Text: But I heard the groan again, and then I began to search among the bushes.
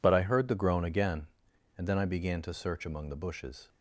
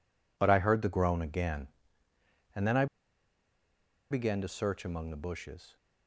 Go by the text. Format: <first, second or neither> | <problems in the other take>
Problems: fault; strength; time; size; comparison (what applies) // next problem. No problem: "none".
first | pauses between "I" and "began"; strong; at 2.8 s; 1.2 s long